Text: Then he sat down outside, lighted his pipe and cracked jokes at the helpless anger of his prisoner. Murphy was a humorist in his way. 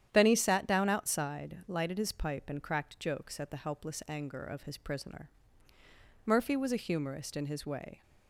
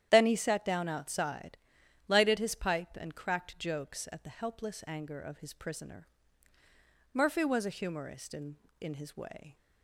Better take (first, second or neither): first